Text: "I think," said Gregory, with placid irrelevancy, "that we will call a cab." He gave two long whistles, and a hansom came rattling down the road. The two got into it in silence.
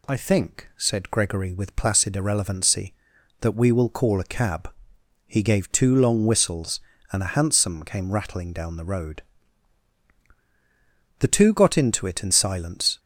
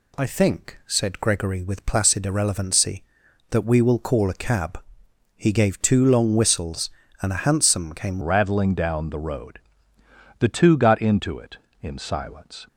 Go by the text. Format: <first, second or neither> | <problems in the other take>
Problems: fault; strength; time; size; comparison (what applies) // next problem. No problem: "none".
first | changes voice at "rattling"; from 8.2 s on; 4.4 s long